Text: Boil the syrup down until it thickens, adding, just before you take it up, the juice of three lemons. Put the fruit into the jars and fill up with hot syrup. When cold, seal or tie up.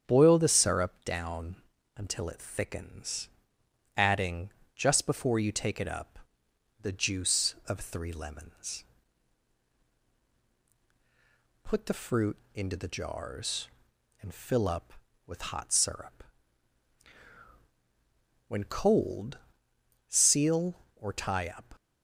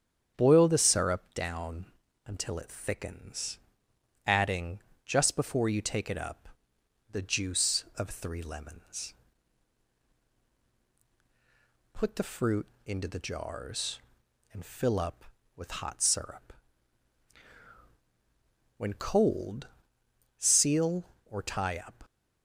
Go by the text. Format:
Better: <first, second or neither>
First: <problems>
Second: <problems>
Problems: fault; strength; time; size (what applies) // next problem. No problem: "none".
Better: neither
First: starts louder than the rest; strong; until 1.0 s; 8.5 dB // pauses between "down" and "until"; at 1.5 s; 0.42 s long // pauses between "fruit" and "into"; slight; at 12.3 s; 0.17 s long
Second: starts louder than the rest; strong; until 1.3 s; 8.5 dB // pauses between "down" and "until"; at 1.8 s; 0.42 s long // pauses between "fruit" and "into"; slight; at 12.6 s; 0.18 s long